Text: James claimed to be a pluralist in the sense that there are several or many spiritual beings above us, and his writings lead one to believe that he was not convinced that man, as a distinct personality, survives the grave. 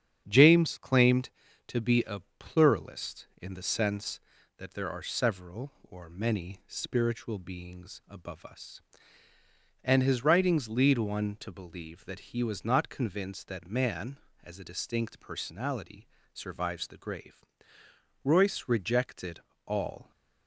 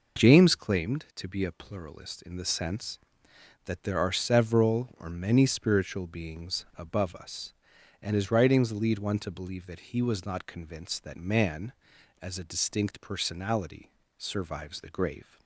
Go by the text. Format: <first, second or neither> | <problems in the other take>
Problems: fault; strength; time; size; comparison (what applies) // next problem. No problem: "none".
second | starts louder than the rest; strong; until 1.2 s; 8.5 dB // pauses between "a" and "pluralist"; slight; at 2.2 s; 0.18 s long // goes on to say "Royce rejected all"; strong; from 18.2 s on; 1.8 s long